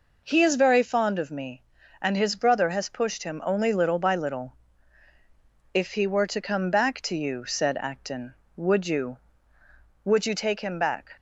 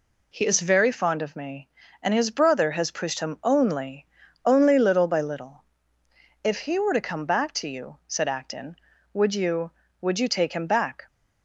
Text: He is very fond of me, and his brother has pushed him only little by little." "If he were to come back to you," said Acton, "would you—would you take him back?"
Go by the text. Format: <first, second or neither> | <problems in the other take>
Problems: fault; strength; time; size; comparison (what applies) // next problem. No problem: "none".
first | says "only" twice; at 4.4 s